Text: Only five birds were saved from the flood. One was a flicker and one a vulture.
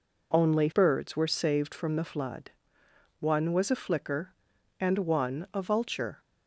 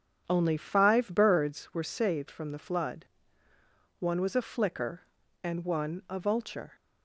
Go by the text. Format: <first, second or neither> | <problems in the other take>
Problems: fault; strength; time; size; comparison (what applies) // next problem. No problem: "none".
second | skips "five"; at 0.7 s